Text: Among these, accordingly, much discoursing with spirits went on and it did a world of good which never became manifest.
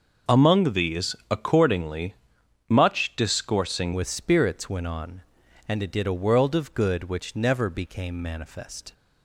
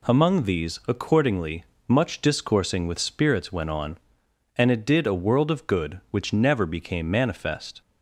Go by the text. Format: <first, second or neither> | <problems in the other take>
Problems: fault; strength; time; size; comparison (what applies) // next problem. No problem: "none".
second | changes voice at "with"; from 3.9 s on; 5.0 s long